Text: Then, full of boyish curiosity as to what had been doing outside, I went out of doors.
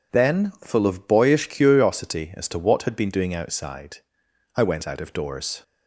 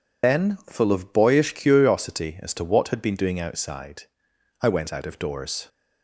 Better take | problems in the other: first | loses the start of "Then"; at 0.2 s; 65 ms

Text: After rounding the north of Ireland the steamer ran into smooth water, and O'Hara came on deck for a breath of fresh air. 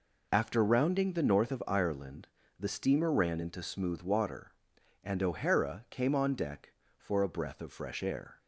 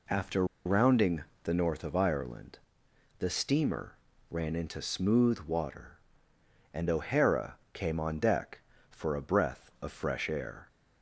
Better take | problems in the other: first | pauses between "After" and "rounding"; slight; at 0.4 s; 0.20 s long // pauses between "rounding" and "the"; slight; at 1.2 s; 0.18 s long // pauses between "Ireland" and "the"; noticeable; at 2.5 s; 0.58 s long; slight in the first // pauses between "steamer" and "ran"; slight; at 3.9 s; 0.34 s long // pauses between "O'Hara" and "came"; slight; at 7.5 s; 0.16 s long

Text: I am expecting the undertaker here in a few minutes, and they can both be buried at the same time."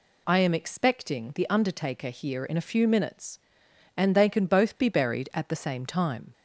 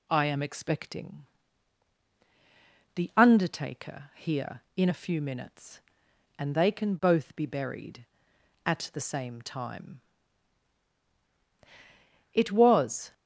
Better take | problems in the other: first | pauses between "expecting" and "the"; strong; at 1.2 s; 1.6 s long // goes on to say "It was"; noticeable; from 12.3 s on; 0.80 s long

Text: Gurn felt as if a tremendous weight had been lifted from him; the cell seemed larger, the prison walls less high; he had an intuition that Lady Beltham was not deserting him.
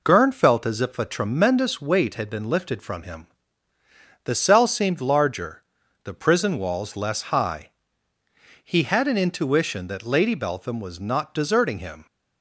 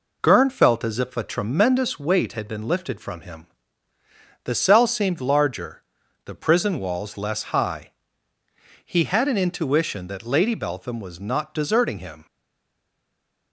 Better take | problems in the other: first | stays silent after the last word; noticeable; from 12.2 s on; 1.3 s long

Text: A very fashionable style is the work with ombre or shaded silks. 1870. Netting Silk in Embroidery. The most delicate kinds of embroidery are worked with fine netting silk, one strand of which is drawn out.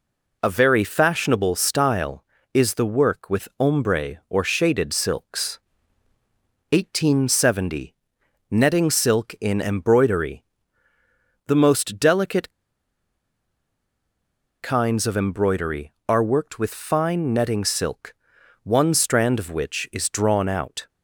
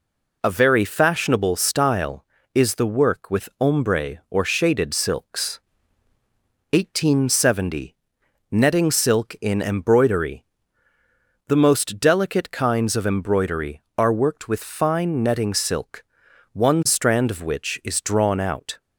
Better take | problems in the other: second | pauses between "delicate" and "kinds"; strong; at 12.5 s; 2.1 s long

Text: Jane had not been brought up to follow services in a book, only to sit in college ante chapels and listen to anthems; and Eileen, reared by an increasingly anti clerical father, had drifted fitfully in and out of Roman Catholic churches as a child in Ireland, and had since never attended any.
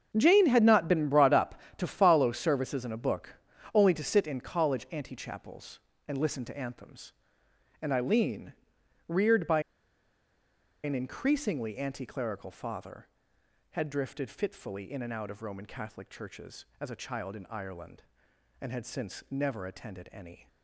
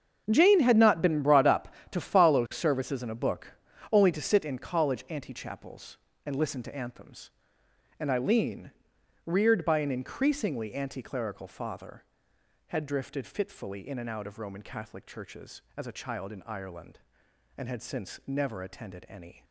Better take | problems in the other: second | starts louder than the rest; until 1.1 s; 7 dB; also in the second // pauses between "by" and "an"; at 9.5 s; 1.2 s long

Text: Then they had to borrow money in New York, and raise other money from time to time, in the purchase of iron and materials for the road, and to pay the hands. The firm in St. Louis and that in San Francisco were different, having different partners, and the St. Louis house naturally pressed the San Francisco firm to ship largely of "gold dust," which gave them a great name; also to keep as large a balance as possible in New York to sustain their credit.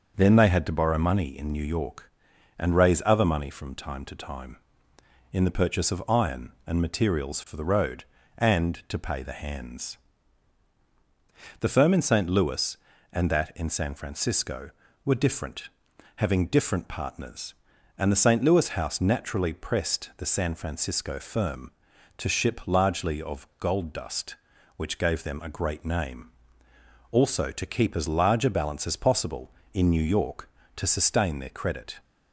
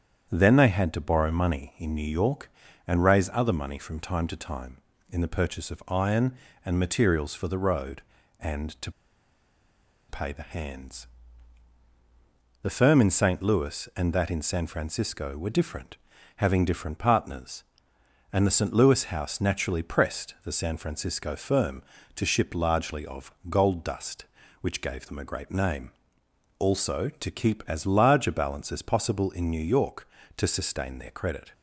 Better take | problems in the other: first | starts louder than the rest; strong; until 1.3 s; 8.5 dB; also in the first // pauses between "to" and "pay"; at 8.9 s; 1.1 s long // pauses between "of" and "gold"; slight; at 23.3 s; 0.16 s long

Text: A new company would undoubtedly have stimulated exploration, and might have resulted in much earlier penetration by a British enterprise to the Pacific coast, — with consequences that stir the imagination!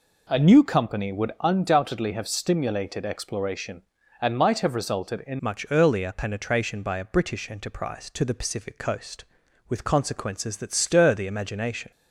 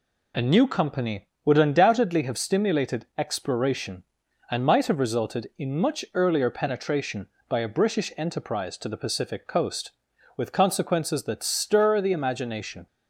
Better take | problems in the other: second | changes voice at "much"; from 5.4 s on; 6.5 s long

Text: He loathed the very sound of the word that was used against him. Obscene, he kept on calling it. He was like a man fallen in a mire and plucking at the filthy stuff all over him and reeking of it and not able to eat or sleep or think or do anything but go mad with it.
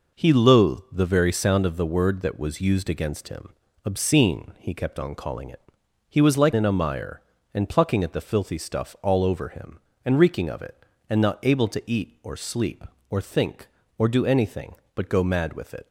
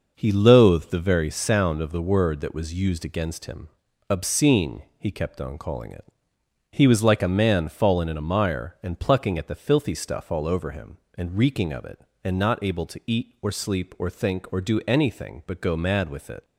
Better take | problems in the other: second | skips "a man fallen"; at 6.5 s

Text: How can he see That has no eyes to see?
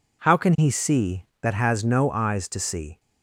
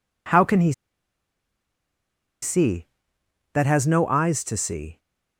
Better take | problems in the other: first | pauses between "he" and "see"; strong; at 0.7 s; 1.6 s long

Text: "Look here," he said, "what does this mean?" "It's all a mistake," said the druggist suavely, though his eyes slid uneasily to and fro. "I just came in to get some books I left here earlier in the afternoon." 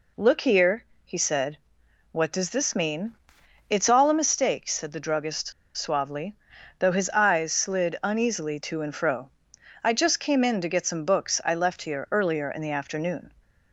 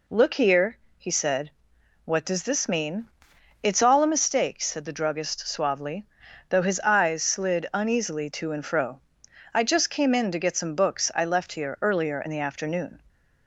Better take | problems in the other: second | pauses between "druggist" and "suavely"; slight; at 5.5 s; 0.25 s long

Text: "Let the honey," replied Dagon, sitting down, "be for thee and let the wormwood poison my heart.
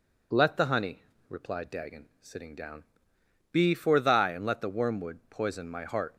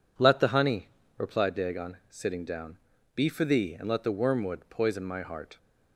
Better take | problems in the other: second | says "thy" for "thee"; at 3.9 s

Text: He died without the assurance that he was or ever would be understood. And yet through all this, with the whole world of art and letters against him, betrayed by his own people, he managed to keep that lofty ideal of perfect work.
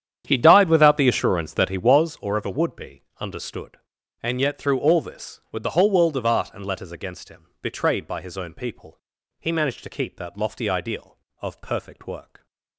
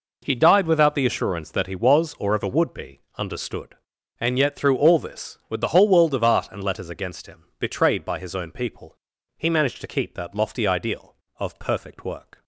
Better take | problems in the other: second | starts louder than the rest; strong; until 2.1 s; 9 dB // pauses between "be" and "understood"; slight; at 3.0 s; 0.16 s long; slight in the second

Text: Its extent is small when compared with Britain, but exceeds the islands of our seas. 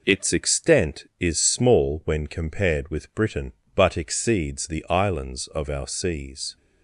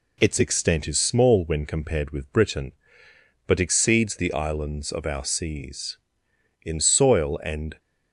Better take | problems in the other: first | goes on to say "In soil and"; noticeable; from 6.6 s on; 1.1 s long

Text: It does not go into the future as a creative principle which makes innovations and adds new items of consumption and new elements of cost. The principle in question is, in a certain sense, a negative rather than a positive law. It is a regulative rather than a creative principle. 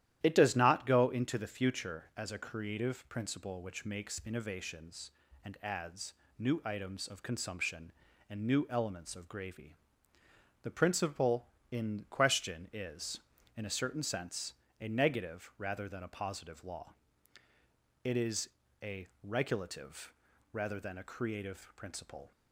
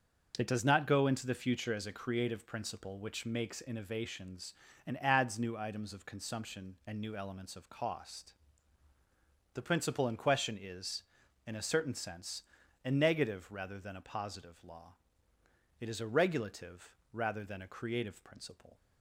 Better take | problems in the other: second | starts louder than the rest; strong; until 1.2 s; 12 dB; also in the second // pauses between "adds" and "new"; slight; at 6.1 s; 0.24 s long // says "gravy" for "cost"; at 9.2 s // pauses between "is" and "a"; slight; at 18.4 s; 0.34 s long // pauses between "a" and "regulative"; slight; at 19.0 s; 0.16 s long // pauses between "regulative" and "rather"; at 20.1 s; 0.40 s long; slight in the second

